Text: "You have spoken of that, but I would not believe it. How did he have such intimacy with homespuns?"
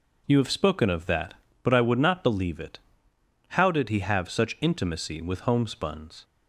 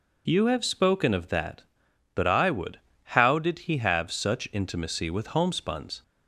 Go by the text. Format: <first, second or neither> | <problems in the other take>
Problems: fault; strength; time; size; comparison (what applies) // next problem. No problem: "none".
first | skips "not believe it"; at 2.9 s